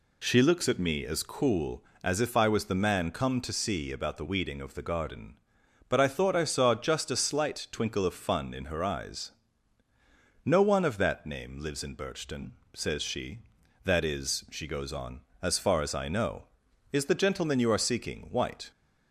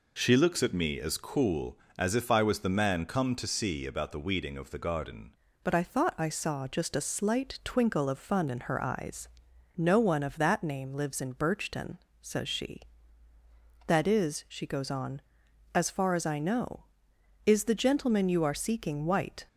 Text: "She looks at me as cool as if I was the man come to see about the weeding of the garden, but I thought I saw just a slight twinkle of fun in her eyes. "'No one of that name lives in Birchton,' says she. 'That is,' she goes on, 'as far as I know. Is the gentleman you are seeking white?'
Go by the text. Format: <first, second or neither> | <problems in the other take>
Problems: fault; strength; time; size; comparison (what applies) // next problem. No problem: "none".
first | changes voice at "but"; from 5.6 s on; 13.8 s long